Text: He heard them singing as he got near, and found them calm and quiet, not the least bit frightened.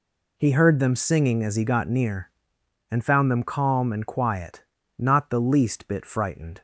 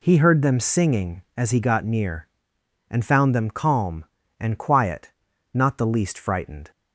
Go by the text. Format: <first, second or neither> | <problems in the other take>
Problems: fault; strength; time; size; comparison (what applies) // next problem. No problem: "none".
first | skips "bit"; at 6.1 s